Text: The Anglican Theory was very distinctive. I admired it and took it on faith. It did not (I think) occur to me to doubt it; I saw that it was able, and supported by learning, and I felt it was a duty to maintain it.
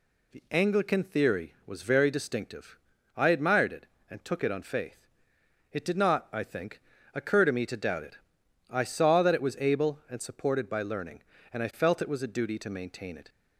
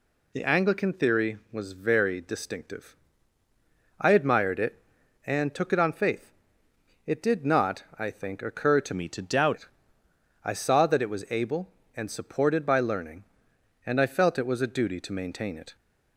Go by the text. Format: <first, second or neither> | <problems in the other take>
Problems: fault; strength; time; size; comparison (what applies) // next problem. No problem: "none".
first | changes voice from "me" to "doubt"; from 8.9 to 9.5 s; 0.6 s long